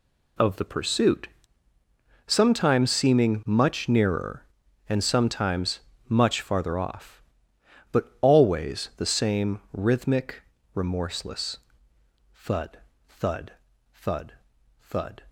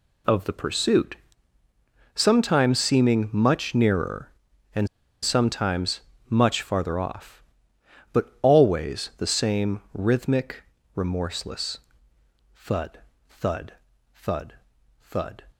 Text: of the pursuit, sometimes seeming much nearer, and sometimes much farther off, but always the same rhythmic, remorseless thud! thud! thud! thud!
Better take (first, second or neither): first